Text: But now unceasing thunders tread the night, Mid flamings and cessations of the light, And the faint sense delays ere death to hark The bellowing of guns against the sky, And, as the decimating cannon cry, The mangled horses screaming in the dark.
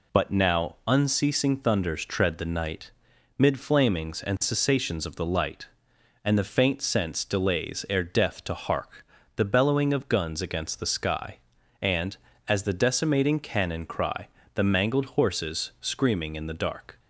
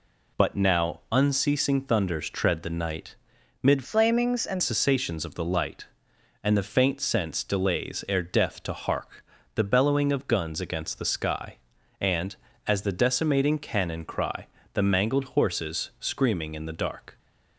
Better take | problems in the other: first | changes voice from "flamings" to "and"; from 3.8 to 4.6 s; 0.8 s long // pauses between "hark" and "The"; slight; at 9.2 s; 0.30 s long; slight in the first

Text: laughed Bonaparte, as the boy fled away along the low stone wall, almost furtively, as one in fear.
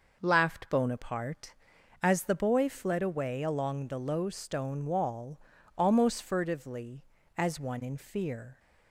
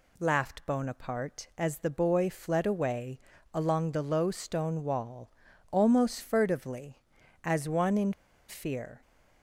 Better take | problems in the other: first | pauses between "away" and "along"; slight; at 3.1 s; 0.34 s long // pauses between "in" and "fear"; slight; at 8.1 s; 0.36 s long

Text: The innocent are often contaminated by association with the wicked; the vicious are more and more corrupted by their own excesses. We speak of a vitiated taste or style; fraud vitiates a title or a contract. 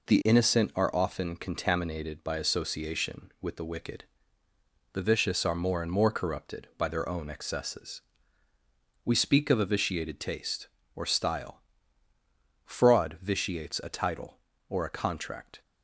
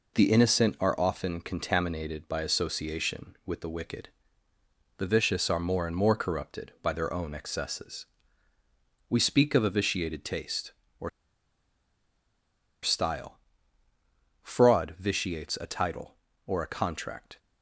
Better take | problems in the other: first | pauses between "or" and "style"; strong; at 11.0 s; 1.7 s long

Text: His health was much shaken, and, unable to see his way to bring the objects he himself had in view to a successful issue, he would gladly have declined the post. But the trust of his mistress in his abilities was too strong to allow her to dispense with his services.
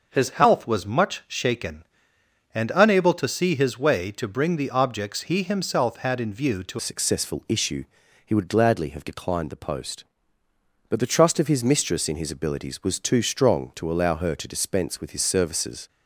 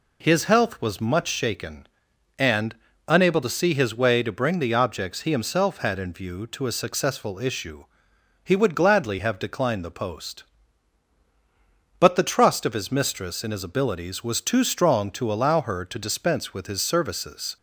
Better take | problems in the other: second | changes voice at "a"; from 6.7 s on; 9.1 s long

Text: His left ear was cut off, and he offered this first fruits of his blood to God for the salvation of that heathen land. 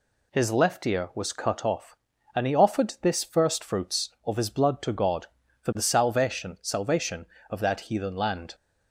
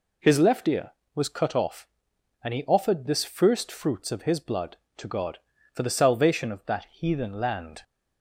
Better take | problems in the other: second | says "salvation" twice; at 6.6 s

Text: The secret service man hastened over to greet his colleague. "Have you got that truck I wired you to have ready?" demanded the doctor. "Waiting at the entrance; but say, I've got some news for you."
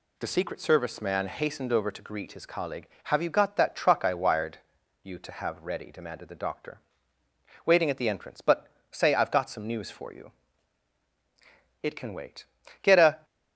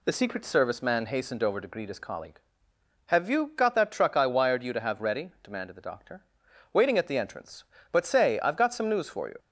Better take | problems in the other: second | pauses between "wired" and "you"; at 4.5 s; 0.44 s long // pauses between "but" and "say"; slight; at 8.6 s; 0.24 s long // goes on to say "It can wait Get a"; from 11.8 s on; 1.4 s long

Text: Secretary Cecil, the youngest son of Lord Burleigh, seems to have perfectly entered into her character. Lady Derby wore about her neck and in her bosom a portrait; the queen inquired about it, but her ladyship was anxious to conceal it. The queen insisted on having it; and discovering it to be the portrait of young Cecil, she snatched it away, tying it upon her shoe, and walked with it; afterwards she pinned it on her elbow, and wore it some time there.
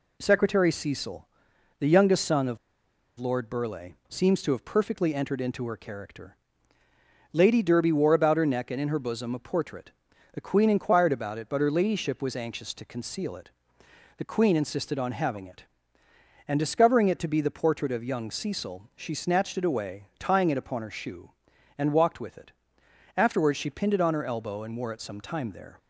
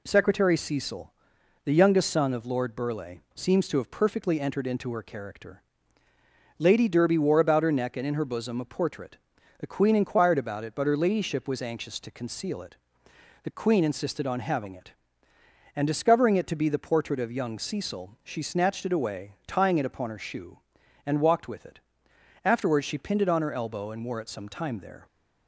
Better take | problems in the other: second | pauses between "of" and "Lord"; noticeable; at 2.5 s; 0.62 s long

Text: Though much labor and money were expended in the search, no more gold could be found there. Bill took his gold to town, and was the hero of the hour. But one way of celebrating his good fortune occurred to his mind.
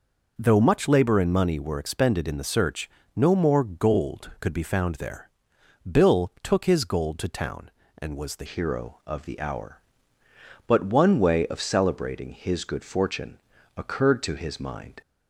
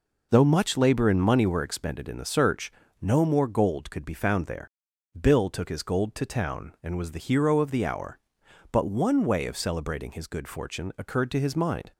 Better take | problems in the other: second | changes voice at "hero"; from 8.4 s on; 6.6 s long // pauses between "fortune" and "occurred"; slight; at 13.3 s; 0.36 s long

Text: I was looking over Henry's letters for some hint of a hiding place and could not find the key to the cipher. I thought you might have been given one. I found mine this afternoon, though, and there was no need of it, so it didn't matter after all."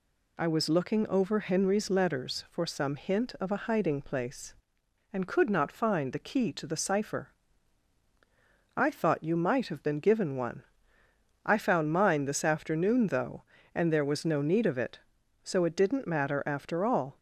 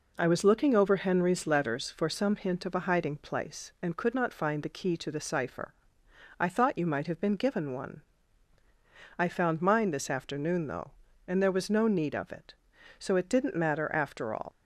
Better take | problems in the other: first | leaves "all" unfinished; at 14.5 s; 130 ms

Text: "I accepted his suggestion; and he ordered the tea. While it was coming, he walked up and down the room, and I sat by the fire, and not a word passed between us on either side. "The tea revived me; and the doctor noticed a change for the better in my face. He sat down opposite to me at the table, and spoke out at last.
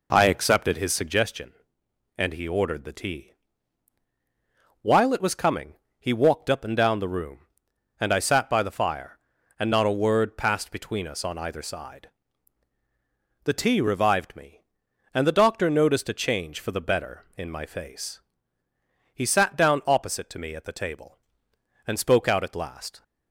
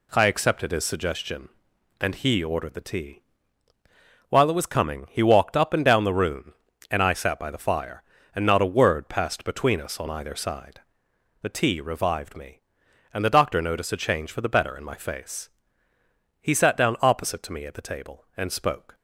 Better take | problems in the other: first | stops before "out at last"; at 18.9 s

